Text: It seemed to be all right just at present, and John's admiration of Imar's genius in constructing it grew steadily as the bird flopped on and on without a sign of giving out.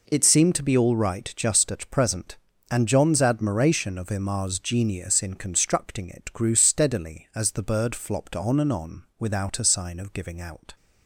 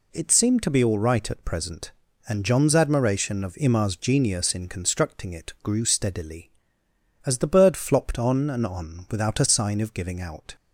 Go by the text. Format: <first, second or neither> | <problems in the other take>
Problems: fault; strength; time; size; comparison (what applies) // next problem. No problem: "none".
first | skips "just"; at 1.2 s